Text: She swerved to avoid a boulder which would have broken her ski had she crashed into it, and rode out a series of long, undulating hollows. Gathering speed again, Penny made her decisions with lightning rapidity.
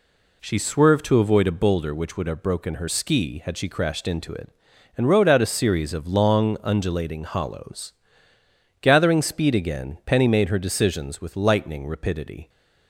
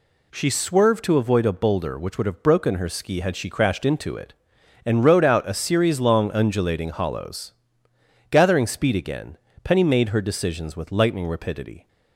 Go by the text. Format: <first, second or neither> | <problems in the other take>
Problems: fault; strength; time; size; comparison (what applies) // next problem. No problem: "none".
first | skips "of"; at 5.9 s